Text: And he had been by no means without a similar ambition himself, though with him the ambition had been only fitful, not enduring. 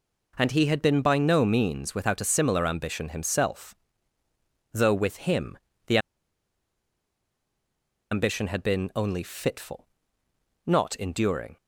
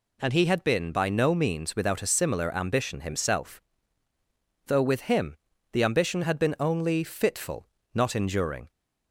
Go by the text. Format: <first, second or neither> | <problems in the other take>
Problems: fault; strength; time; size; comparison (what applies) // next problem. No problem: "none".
second | pauses between "him" and "the"; slight; at 5.5 s; 0.30 s long; slight in the second // pauses between "the" and "ambition"; strong; at 5.9 s; 2.1 s long